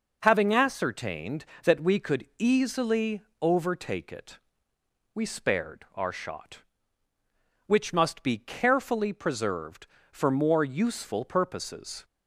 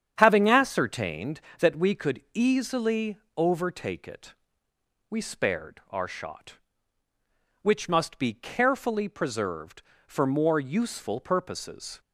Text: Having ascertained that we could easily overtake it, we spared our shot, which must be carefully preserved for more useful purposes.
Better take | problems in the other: first | starts louder than the rest; strong; until 1.4 s; 8.5 dB // pauses between "easily" and "overtake"; slight; at 3.1 s; 0.18 s long; slight in the first

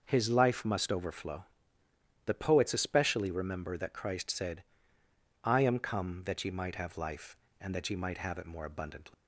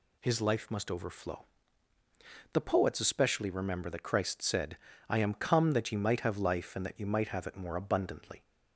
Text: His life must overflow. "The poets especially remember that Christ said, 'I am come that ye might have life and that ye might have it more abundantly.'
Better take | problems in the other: second | starts louder than the rest; noticeable; until 1.0 s; 6 dB // leaves "abundantly" unfinished; at 9.1 s; 150 ms

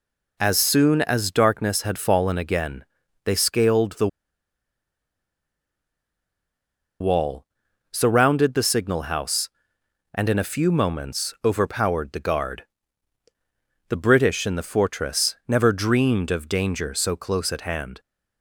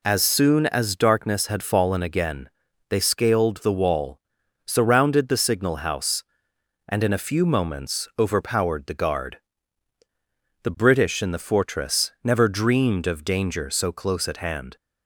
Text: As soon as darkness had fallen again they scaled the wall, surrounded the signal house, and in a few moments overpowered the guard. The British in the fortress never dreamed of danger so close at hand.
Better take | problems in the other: second | pauses between "again" and "they"; at 2.8 s; 0.40 s long; also in the second // pauses between "the" and "wall"; strong; at 4.0 s; 2.9 s long

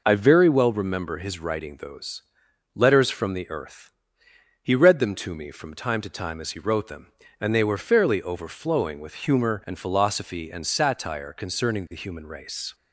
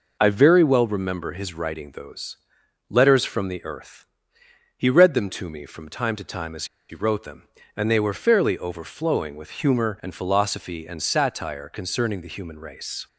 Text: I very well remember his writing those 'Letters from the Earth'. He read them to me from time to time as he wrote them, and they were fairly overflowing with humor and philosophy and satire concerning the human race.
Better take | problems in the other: first | pauses between "those" and "Letters"; noticeable; at 2.3 s; 0.52 s long; noticeable in the first // pauses between "as" and "he"; slight; at 6.6 s; 0.23 s long

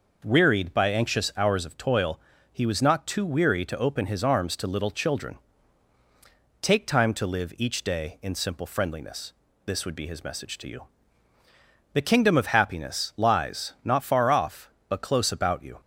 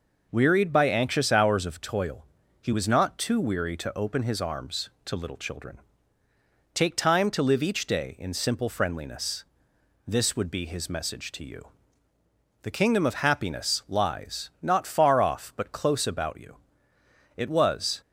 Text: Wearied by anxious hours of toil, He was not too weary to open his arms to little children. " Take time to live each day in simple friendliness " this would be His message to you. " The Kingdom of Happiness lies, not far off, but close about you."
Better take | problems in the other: first | goes on to say "It was"; noticeable; from 17.3 s on; 0.64 s long

